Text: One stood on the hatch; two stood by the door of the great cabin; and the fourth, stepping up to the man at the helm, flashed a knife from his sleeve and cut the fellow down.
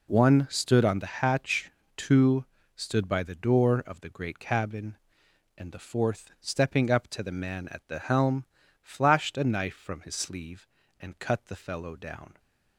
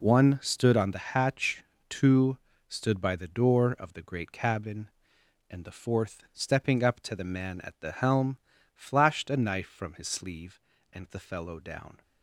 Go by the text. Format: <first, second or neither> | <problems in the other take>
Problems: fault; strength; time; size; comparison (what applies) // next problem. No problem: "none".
first | pauses between "two" and "stood"; slight; at 2.3 s; 0.28 s long; slight in the first // skips "cut"; at 11.1 s